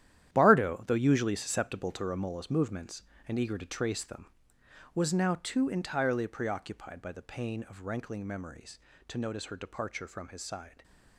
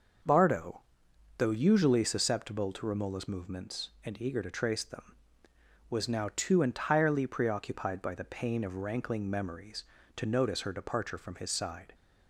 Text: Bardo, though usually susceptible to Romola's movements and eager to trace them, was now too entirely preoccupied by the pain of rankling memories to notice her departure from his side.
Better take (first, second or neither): second